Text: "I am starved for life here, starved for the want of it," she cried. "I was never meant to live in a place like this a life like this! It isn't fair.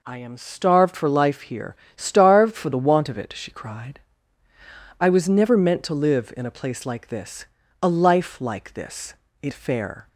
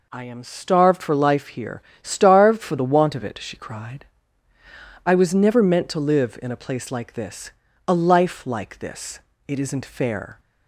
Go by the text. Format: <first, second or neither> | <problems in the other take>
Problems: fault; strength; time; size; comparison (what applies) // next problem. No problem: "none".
second | pauses between "this" and "a"; slight; at 7.4 s; 0.34 s long; slight in the second // skips "isn't"; at 9.5 s